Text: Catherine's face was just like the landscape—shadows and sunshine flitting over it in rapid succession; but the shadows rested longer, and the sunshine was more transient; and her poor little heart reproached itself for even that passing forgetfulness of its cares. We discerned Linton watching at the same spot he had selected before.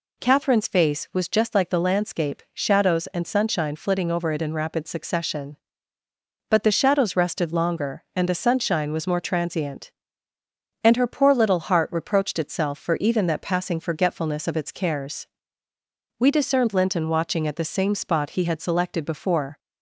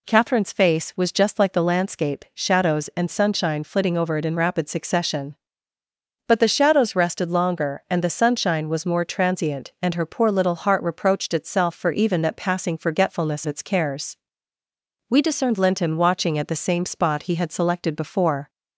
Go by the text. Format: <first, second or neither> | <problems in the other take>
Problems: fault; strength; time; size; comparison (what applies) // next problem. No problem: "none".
first | skips "of"; at 13.4 s